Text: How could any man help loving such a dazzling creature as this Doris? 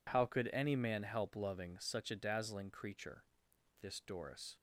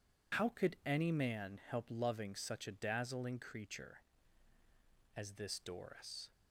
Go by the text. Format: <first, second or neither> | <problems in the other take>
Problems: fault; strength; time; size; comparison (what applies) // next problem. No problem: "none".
second | skips "as"; at 3.5 s